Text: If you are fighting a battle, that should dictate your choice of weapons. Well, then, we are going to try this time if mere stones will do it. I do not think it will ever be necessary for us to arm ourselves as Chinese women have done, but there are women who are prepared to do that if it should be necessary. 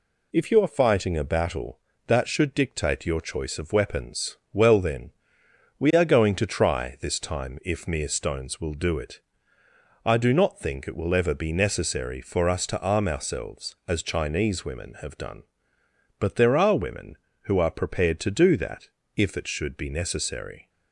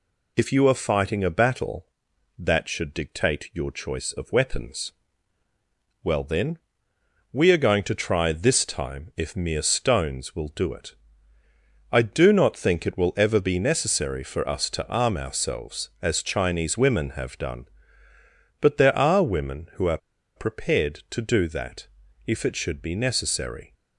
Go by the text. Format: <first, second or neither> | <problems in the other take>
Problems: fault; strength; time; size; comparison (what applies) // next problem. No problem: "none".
first | pauses between "are" and "prepared"; at 19.9 s; 0.39 s long // pauses between "that" and "if"; at 21.8 s; 0.38 s long; slight in the first